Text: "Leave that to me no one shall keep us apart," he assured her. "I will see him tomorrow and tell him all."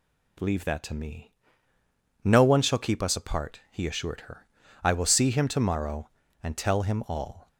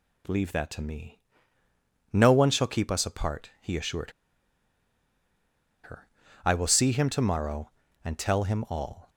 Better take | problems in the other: first | pauses between "me" and "no"; noticeable; at 1.1 s; 0.92 s long; noticeable in the first // pauses between "assured" and "her"; strong; at 4.1 s; 1.7 s long

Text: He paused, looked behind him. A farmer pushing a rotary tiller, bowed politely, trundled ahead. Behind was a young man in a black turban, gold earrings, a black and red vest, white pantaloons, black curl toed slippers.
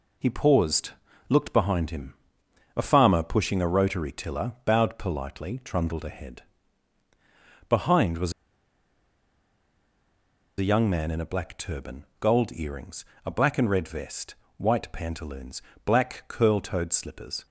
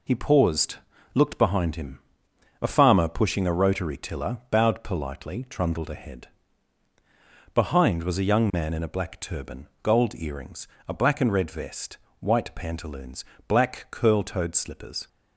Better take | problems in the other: second | pauses between "was" and "a"; strong; at 8.3 s; 2.2 s long

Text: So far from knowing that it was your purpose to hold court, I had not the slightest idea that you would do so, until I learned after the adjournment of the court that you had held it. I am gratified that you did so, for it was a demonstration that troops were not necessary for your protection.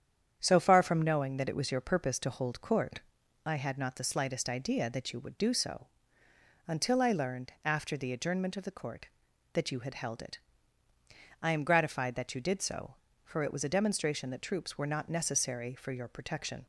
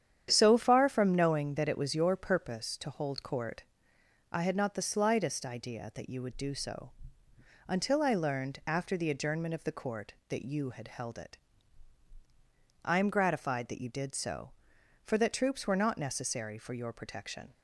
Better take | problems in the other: first | starts louder than the rest; strong; until 1.3 s; 9.5 dB; strong in the first // skips "it was a demonstration"; at 15.1 s

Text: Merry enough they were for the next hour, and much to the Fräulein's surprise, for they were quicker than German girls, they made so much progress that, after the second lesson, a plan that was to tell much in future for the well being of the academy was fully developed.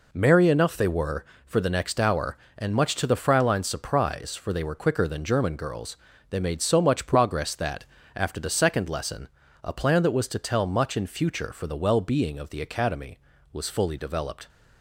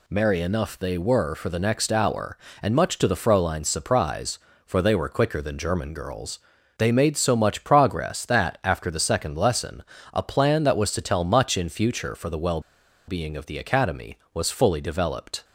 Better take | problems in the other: first | pauses between "well" and "being"; noticeable; at 12.6 s; 0.47 s long

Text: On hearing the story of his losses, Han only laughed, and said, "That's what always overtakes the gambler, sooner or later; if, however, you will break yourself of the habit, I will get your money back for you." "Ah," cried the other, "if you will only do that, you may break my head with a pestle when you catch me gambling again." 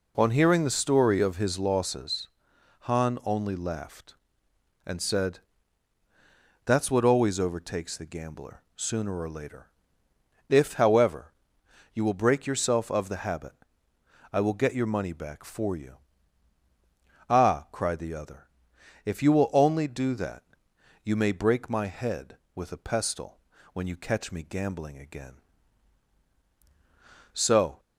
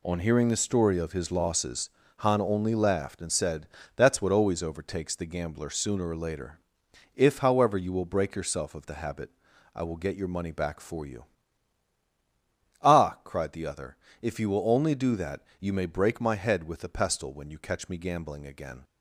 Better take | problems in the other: second | pauses between "pestle" and "when"; slight; at 23.3 s; 0.36 s long // goes on to say "So"; slight; from 27.3 s on; 0.46 s long

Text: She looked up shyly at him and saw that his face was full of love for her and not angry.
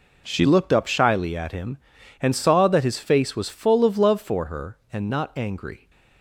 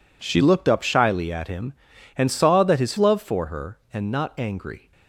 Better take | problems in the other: first | skips "face was full of"; at 2.9 s

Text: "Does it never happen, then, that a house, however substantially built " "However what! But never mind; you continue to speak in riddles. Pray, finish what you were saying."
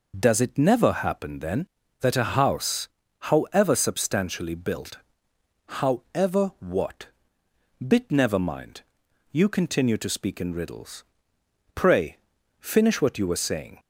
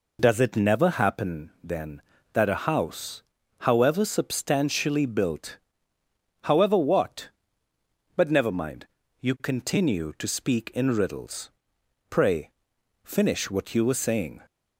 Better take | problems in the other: second | says "Bit" for "But"; at 7.8 s

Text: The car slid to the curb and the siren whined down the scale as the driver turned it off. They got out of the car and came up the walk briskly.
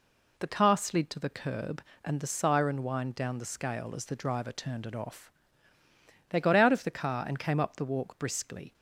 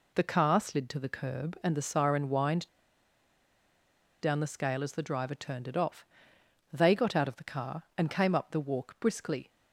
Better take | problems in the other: first | pauses between "whined" and "down"; strong; at 2.6 s; 1.5 s long

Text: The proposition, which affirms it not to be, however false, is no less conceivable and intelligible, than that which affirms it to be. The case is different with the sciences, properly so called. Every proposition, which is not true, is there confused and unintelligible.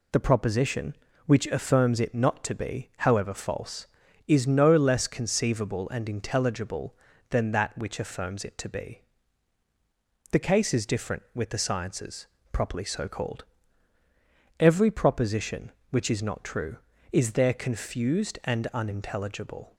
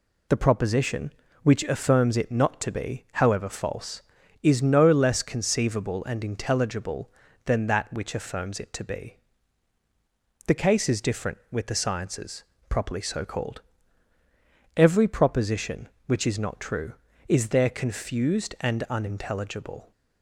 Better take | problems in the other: neither | none

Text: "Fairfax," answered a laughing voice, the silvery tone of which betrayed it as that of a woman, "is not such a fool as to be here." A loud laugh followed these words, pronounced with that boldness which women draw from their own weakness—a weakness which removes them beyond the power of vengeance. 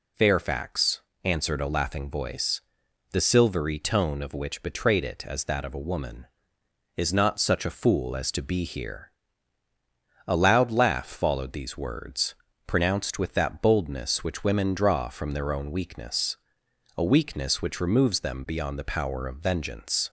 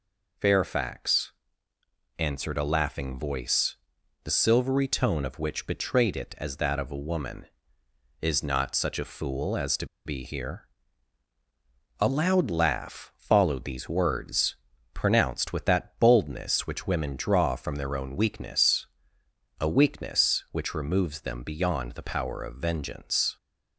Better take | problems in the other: first | pauses between "to" and "be"; slight; at 9.8 s; 0.18 s long

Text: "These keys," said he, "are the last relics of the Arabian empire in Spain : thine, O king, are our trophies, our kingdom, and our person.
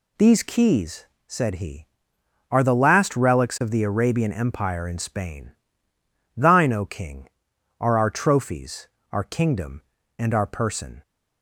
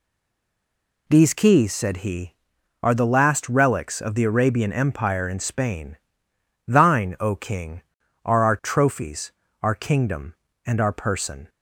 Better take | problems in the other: first | stays silent before the first word; until 1.0 s; 1.0 s long

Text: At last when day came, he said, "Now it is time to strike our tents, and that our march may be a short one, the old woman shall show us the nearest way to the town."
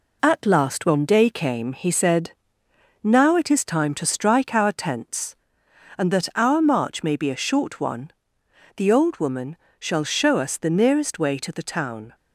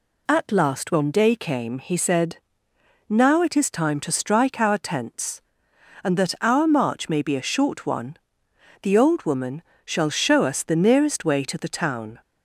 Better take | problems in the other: second | gets quieter; throughout; 4 dB // pauses between "woman" and "shall"; slight; at 9.5 s; 0.24 s long; slight in the second

